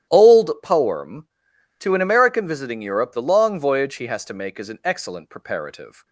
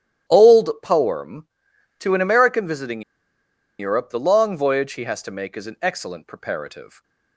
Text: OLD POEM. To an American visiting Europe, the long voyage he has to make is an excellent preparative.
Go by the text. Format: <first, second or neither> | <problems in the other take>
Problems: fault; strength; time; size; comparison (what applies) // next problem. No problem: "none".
first | starts louder than the rest; strong; until 1.4 s; 12 dB; strong in the first // pauses between "visiting" and "Europe"; noticeable; at 3.0 s; 0.78 s long